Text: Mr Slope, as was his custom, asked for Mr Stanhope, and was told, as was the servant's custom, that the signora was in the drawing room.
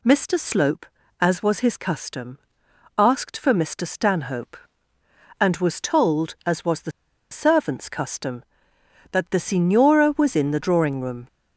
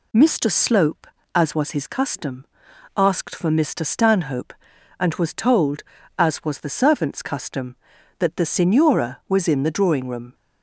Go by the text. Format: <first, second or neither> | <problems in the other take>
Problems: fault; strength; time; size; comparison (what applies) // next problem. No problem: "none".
second | pauses between "the" and "servant's"; at 6.9 s; 0.40 s long